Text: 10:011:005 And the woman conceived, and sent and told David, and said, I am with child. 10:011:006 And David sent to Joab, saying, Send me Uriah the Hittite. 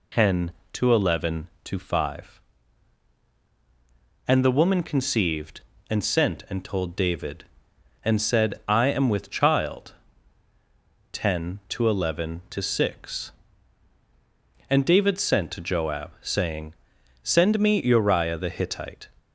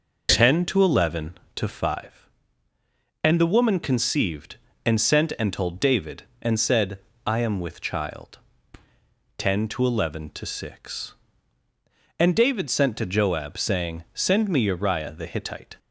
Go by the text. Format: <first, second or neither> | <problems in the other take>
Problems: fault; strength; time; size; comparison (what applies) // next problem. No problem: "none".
neither | none